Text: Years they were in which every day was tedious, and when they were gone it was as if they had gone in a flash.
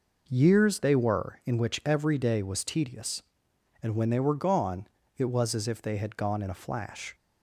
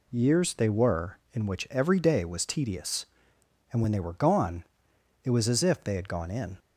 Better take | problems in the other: first | pauses between "gone" and "it"; noticeable; at 4.6 s; 0.62 s long; slight in the first // stops before "a flash"; at 6.5 s

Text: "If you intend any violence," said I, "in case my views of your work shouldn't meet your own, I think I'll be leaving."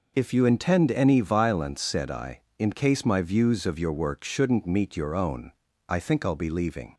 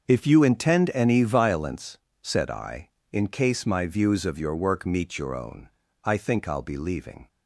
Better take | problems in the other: first | starts louder than the rest; until 1.1 s; 6.5 dB // skips "shouldn't"; at 4.8 s

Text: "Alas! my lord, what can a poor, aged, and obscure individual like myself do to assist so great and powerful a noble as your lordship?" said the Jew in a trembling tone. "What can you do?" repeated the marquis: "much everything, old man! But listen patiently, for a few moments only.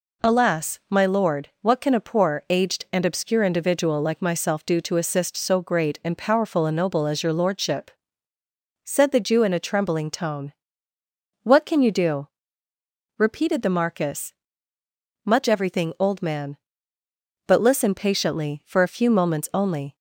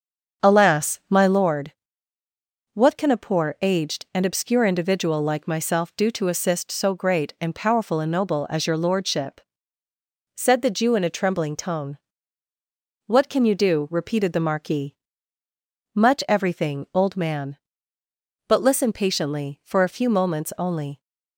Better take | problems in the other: first | starts louder than the rest; until 1.5 s; 7 dB

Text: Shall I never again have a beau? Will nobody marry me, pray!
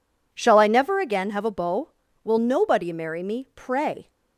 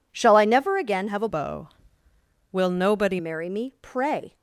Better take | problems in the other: first | changes voice from "beau" to "nobody"; from 1.2 to 3.1 s; 1.9 s long

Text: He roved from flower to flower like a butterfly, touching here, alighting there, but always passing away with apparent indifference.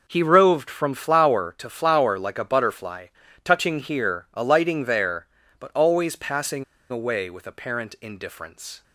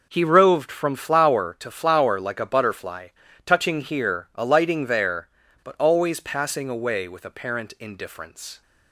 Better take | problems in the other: second | pauses between "passing" and "away"; slight; at 6.6 s; 0.26 s long

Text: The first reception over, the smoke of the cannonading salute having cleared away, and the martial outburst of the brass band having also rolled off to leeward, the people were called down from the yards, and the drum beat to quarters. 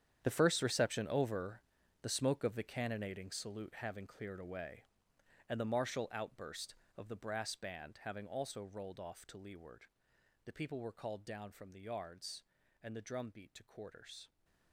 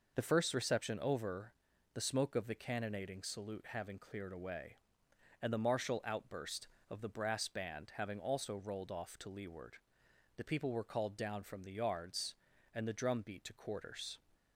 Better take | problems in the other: second | gets quieter; strong; throughout; 14.5 dB

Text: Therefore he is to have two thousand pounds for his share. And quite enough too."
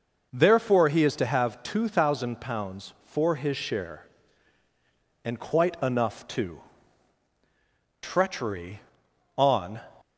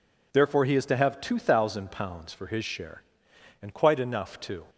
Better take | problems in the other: second | goes on to say "Treachery on"; strong; from 8.0 s on; 1.7 s long

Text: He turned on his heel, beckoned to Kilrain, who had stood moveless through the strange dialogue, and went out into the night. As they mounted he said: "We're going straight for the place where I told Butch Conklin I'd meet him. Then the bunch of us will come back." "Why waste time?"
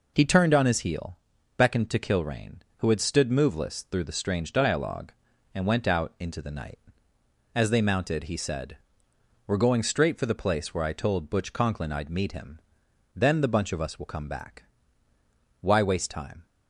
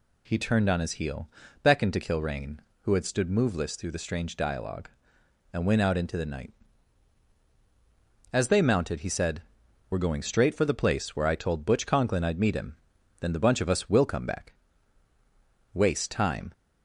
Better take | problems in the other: first | skips "Why"; at 15.1 s

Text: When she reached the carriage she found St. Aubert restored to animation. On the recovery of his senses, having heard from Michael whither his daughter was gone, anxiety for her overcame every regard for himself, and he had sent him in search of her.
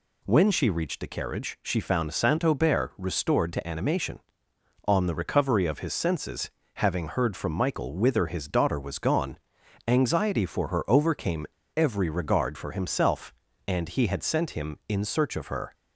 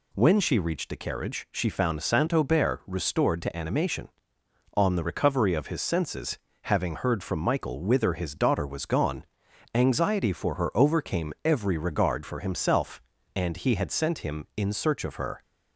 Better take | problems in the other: second | pauses between "overcame" and "every"; slight; at 11.4 s; 0.32 s long

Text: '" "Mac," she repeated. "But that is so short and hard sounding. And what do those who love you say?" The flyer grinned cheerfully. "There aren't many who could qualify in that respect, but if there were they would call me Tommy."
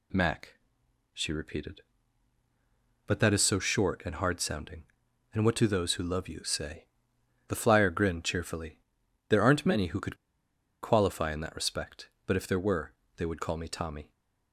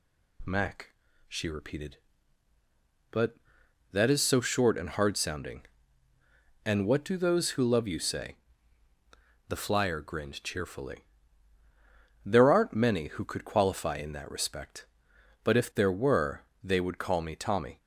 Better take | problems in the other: second | pauses between "could" and "qualify"; noticeable; at 10.1 s; 0.67 s long // pauses between "were" and "they"; slight; at 12.9 s; 0.24 s long; slight in the second

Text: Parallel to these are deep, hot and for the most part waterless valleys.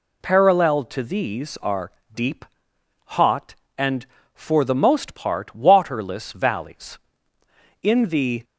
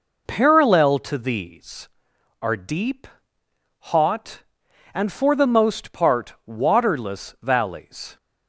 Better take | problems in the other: second | pauses between "are" and "deep"; slight; at 1.9 s; 0.22 s long // goes on to say "In the"; noticeable; from 7.8 s on; 0.62 s long

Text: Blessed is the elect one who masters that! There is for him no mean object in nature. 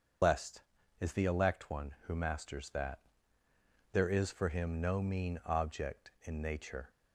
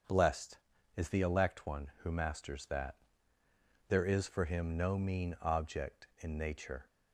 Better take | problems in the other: second | loses the start of "Blessed"; at 0.2 s; 120 ms // starts louder than the rest; until 1.6 s; 7 dB; strong in the second

